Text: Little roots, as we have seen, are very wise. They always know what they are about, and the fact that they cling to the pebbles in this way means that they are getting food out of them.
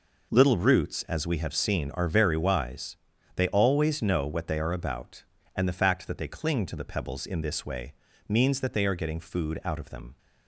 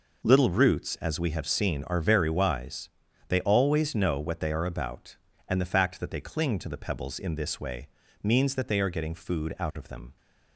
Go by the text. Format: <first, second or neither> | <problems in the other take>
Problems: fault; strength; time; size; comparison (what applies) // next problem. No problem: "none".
neither | pauses between "way" and "means"; slight; the same in both